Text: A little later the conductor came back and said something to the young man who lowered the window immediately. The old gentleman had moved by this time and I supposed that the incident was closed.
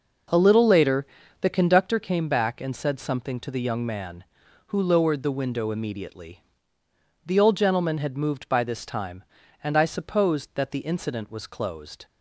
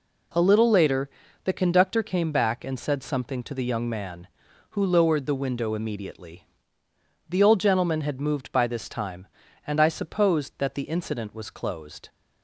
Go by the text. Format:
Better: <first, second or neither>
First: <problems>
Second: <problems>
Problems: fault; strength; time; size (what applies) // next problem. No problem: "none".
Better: second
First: starts louder than the rest; noticeable; until 2.0 s; 5.5 dB // pauses between "later" and "the"; slight; at 1.0 s; 0.34 s long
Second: pauses between "later" and "the"; slight; at 1.1 s; 0.34 s long